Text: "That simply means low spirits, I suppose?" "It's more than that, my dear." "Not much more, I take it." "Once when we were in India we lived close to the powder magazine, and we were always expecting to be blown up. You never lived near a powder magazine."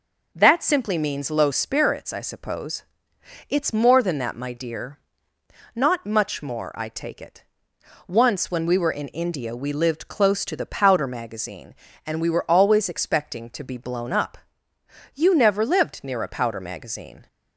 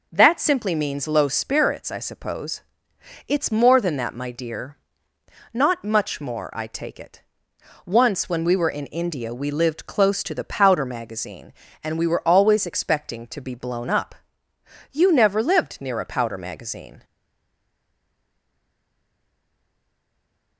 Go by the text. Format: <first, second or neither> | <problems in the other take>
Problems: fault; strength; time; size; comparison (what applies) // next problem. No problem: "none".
first | stays silent after the last word; strong; from 17.0 s on; 3.5 s long